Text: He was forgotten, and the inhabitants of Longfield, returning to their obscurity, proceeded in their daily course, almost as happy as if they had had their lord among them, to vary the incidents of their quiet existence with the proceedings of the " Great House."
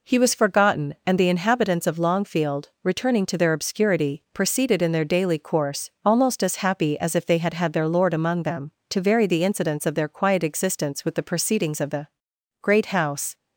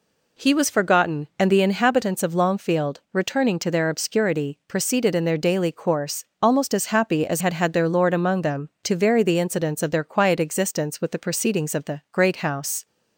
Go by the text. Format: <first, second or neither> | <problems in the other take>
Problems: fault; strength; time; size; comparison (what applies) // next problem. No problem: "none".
first | skips "if they"; at 7.4 s